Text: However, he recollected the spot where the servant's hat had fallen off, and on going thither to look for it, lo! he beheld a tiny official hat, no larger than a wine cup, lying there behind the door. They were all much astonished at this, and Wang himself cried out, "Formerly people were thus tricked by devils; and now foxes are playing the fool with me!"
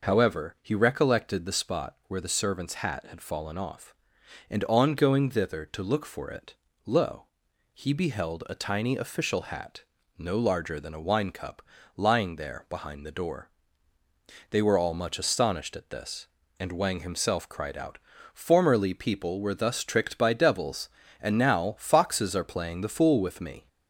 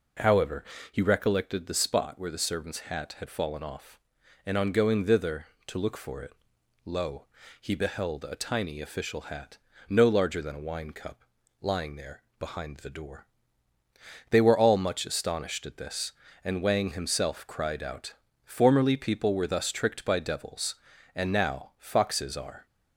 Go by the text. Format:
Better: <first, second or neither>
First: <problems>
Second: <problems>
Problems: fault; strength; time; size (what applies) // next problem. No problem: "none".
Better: first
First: none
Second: pauses between "there" and "behind"; slight; at 12.2 s; 0.18 s long // stops before "playing the fool with me"; at 22.6 s